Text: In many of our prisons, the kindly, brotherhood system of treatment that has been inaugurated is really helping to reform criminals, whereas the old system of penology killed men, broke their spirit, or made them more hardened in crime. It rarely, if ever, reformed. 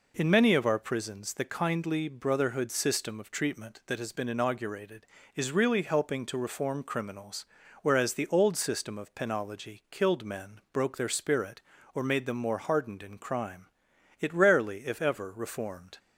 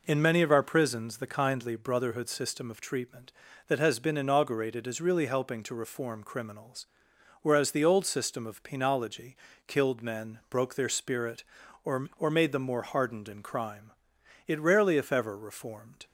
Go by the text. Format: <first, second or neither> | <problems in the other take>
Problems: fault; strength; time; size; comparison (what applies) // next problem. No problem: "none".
first | pauses between "penology" and "killed"; slight; at 9.3 s; 0.30 s long // says "or" twice; at 12.1 s